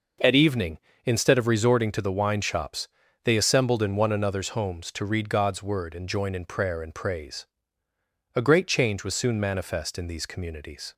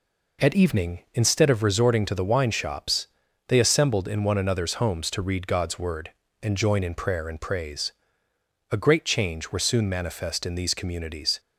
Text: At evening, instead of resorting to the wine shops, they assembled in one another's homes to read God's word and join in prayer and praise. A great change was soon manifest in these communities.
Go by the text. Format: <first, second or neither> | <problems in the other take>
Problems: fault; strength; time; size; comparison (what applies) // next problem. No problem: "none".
first | says "were" for "was"; at 9.5 s